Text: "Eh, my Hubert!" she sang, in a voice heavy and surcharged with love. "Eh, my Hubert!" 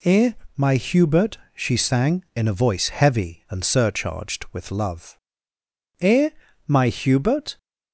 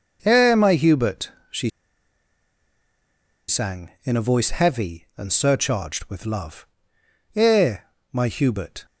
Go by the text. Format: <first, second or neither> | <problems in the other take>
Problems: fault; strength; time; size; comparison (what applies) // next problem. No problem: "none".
first | pauses between "she" and "sang"; strong; at 1.7 s; 1.7 s long